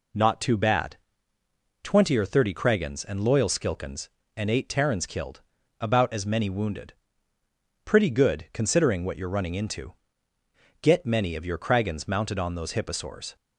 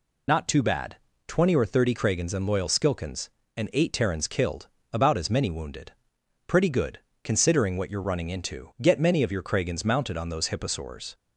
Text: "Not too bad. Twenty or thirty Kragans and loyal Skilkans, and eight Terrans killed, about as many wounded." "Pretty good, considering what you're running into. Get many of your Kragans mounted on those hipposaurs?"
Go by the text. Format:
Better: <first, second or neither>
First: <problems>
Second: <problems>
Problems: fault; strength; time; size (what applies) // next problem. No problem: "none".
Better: first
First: none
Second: loses the start of "Not"; at 0.2 s; 40 ms